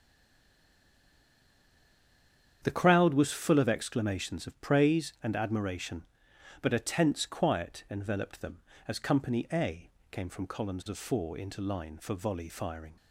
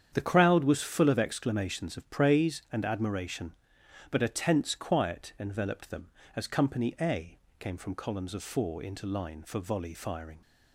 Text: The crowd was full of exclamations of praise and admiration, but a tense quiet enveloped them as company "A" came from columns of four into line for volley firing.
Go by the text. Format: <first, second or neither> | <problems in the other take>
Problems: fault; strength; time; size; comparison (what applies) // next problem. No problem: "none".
second | stays silent before the first word; strong; until 2.6 s; 2.6 s long // starts louder than the rest; strong; until 3.6 s; 8.5 dB; strong in the second // pauses between "A" and "came"; slight; at 9.8 s; 0.22 s long; slight in the second